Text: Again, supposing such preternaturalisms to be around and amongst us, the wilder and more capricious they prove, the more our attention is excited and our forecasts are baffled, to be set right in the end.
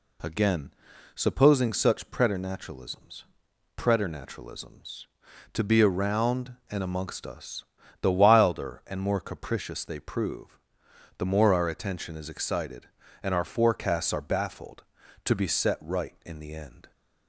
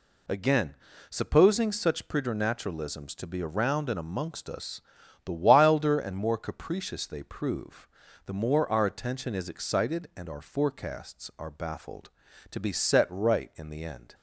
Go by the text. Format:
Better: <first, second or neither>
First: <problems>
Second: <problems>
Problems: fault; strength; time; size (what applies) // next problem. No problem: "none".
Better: second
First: says "preternaturalisms" twice; at 3.7 s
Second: none